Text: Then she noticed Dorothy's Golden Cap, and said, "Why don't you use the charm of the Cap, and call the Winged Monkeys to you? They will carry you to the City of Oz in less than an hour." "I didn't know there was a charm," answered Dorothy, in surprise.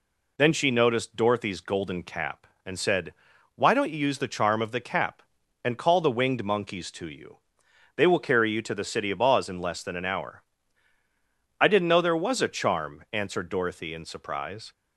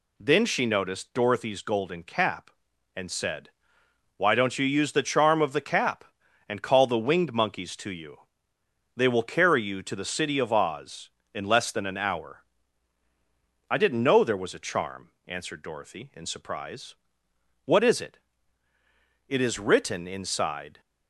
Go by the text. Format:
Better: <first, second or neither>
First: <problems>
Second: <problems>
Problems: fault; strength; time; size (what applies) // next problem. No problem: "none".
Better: first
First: none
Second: goes on to say "What is it It is written inside"; strong; from 17.6 s on; 3.1 s long